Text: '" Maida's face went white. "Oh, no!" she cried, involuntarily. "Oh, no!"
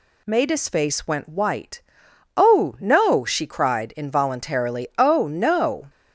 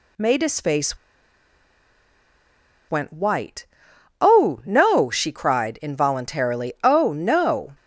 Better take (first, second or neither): first